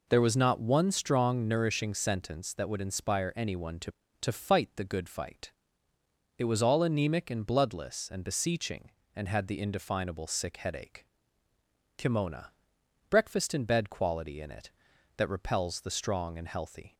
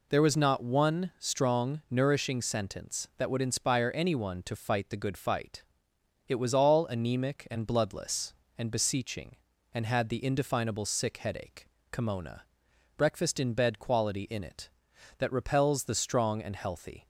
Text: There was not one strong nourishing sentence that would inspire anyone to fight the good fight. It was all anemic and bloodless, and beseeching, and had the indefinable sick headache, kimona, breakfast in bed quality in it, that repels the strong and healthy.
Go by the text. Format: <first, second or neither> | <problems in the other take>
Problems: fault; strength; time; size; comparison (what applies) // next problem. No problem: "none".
second | says "to" twice; at 4.2 s